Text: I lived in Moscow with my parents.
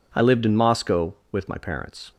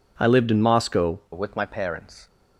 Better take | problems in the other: first | changes voice at "with"; from 1.3 s on; 0.9 s long

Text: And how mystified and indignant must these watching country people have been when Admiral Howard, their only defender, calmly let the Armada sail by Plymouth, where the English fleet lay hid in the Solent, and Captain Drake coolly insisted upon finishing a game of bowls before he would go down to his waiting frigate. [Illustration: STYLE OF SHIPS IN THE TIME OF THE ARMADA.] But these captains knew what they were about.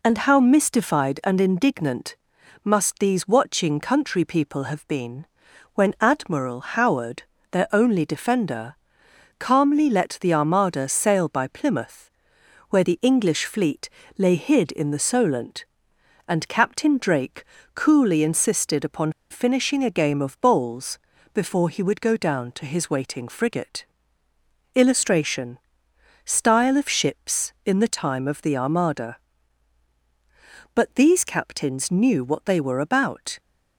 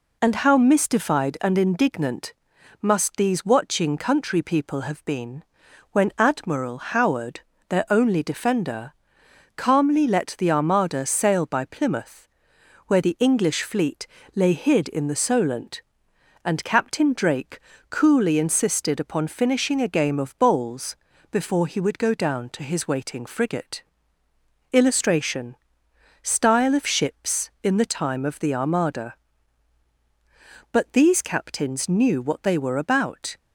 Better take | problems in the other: second | pauses between "indignant" and "must"; noticeable; at 2.1 s; 0.48 s long; noticeable in the second // pauses between "been" and "when"; noticeable; at 5.2 s; 0.48 s long; noticeable in the second // pauses between "fleet" and "lay"; slight; at 13.8 s; 0.28 s long; slight in the second // pauses between "Drake" and "coolly"; slight; at 17.4 s; 0.32 s long; slight in the second // pauses between "upon" and "finishing"; slight; at 19.1 s; 0.19 s long // pauses between "bowls" and "before"; slight; at 20.9 s; 0.34 s long; slight in the second

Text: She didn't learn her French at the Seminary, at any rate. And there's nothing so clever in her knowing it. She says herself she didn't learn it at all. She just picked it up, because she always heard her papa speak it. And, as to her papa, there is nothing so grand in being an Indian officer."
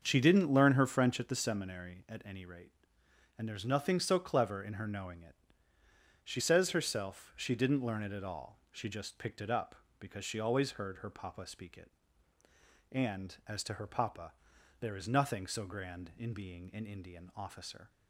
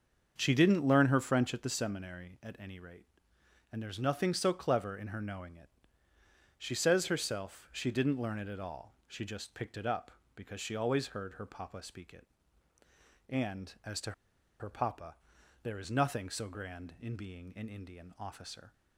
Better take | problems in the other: first | starts louder than the rest; until 1.3 s; 7 dB; also in the first // pauses between "to" and "her"; noticeable; at 14.1 s; 0.48 s long

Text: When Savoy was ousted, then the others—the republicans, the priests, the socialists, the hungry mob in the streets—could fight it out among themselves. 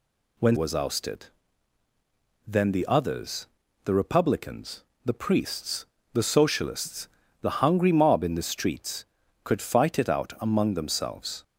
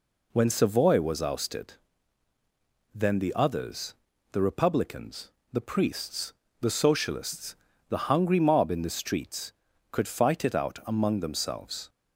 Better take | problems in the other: second | skips "Savoy"; at 0.5 s

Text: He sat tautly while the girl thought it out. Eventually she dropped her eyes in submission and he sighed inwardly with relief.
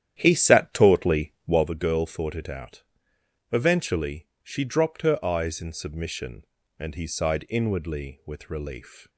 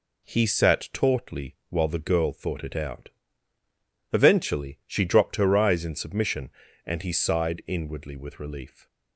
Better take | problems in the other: second | starts louder than the rest; strong; until 1.7 s; 10.5 dB // pauses between "Eventually" and "she"; slight; at 4.2 s; 0.16 s long

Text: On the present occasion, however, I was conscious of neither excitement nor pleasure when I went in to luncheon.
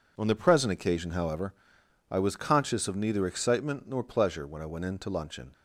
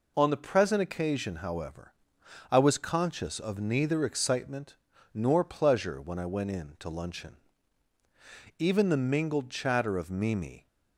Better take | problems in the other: first | pauses between "excitement" and "nor"; slight; at 4.7 s; 0.36 s long // goes on to say "Even the mingled chatter of Mimi"; strong; from 8.6 s on; 2.0 s long

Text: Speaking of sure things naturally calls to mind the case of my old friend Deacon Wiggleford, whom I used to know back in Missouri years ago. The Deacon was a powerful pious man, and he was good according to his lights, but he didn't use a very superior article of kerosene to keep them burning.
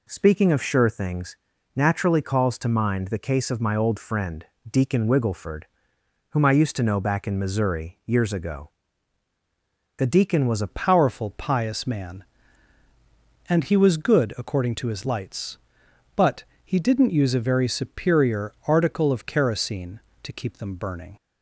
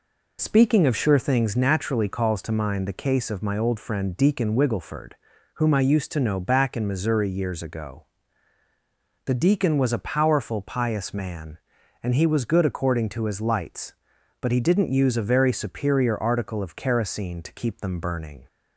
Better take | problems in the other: second | pauses between "things" and "naturally"; at 1.3 s; 0.40 s long // pauses between "friend" and "Deacon"; slight; at 4.4 s; 0.24 s long // changes voice at "powerful"; from 10.7 s on; 10.4 s long // pauses between "but" and "he"; slight; at 16.4 s; 0.22 s long

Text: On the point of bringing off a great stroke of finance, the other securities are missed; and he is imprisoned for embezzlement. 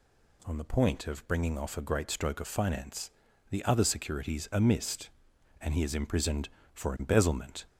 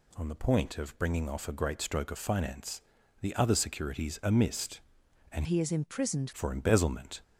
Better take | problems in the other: first | changes voice from "he" to "imprisoned"; from 5.4 to 6.3 s; 0.9 s long

